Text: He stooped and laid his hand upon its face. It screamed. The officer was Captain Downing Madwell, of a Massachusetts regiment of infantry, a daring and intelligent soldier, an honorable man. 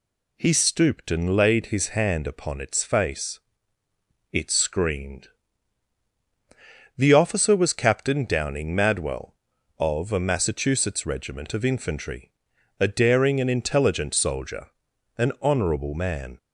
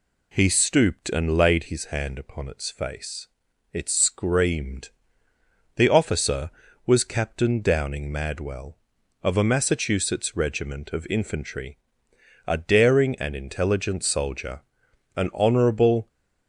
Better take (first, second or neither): first